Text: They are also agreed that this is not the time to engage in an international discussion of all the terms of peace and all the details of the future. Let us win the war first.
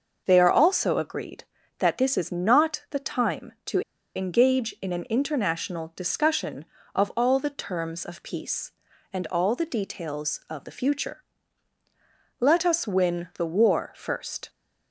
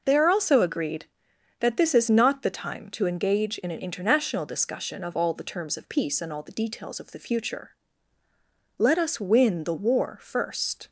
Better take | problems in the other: second | starts louder than the rest; noticeable; until 1.2 s; 6 dB // pauses between "to" and "engage"; slight; at 3.8 s; 0.34 s long

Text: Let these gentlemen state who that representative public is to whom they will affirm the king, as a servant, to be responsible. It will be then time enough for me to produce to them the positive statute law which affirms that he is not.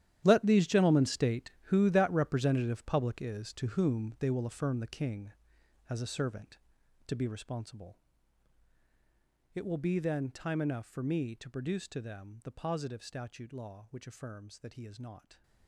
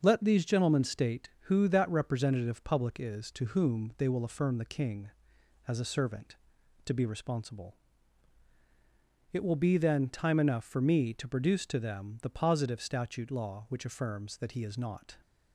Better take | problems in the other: second | gets quieter; strong; throughout; 15 dB // starts louder than the rest; strong; until 1.2 s; 11.5 dB; also in the second

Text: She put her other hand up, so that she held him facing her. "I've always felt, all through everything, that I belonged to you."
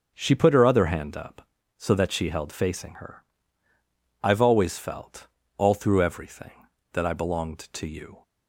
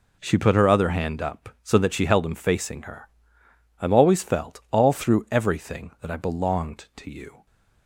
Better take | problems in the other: second | skips "him"; at 2.5 s

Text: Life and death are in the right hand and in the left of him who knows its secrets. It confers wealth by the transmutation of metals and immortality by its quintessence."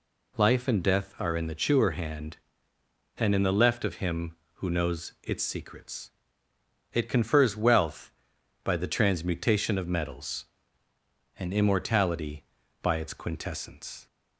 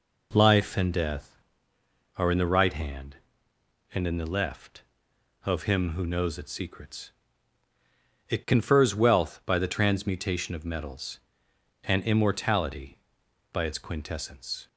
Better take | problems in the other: second | says "chewer" for "right"; at 1.5 s

